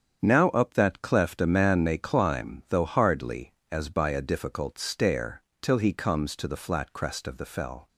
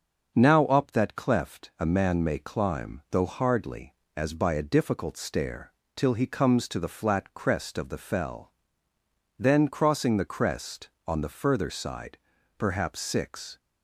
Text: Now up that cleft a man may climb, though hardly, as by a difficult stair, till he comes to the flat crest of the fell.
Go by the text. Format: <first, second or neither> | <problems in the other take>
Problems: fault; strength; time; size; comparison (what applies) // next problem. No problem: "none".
first | starts louder than the rest; until 1.3 s; 7 dB; strong in the first // goes on to say "Then crossing the crest on the further side perhaps six"; strong; from 9.3 s on; 4.2 s long